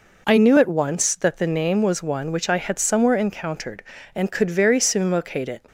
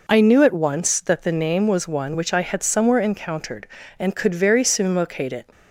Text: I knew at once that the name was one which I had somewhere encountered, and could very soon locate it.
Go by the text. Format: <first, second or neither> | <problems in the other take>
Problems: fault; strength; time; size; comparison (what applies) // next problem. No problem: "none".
neither | none